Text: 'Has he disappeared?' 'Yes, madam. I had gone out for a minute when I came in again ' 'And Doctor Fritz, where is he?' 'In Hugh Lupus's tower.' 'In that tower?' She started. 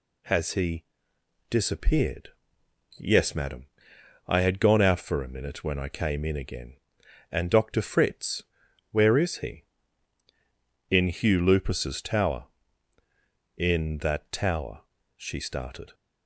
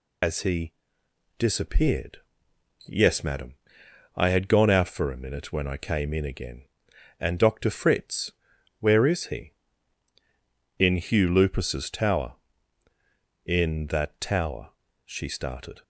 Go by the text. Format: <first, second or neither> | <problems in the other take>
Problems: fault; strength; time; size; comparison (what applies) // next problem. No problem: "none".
first | loses the start of "Has"; at 0.2 s; 120 ms // pauses between "he" and "disappeared"; noticeable; at 0.7 s; 0.66 s long; noticeable in the first